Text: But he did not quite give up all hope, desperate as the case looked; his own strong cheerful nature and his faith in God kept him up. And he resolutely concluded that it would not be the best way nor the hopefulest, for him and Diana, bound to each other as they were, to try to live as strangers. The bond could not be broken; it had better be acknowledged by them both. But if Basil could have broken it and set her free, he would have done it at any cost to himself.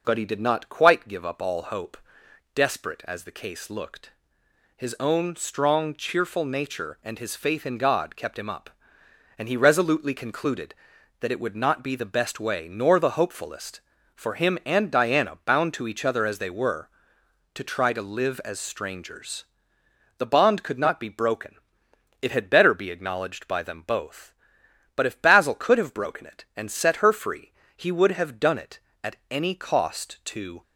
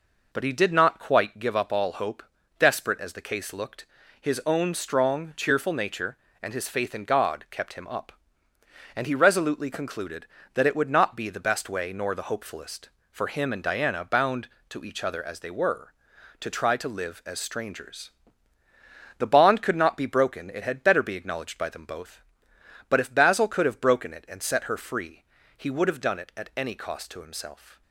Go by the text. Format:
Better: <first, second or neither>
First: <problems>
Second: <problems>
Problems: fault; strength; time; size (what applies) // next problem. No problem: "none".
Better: second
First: stops before "himself"; at 30.6 s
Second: none